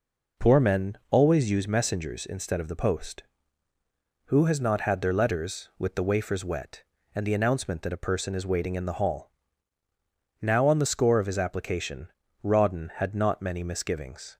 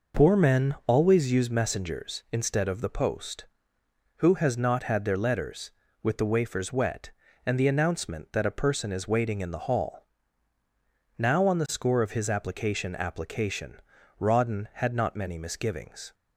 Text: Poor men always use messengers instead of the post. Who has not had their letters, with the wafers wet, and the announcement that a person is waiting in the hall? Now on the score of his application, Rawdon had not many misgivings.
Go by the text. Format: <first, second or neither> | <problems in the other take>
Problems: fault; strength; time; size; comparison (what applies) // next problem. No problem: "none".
first | says "application" twice; at 12.9 s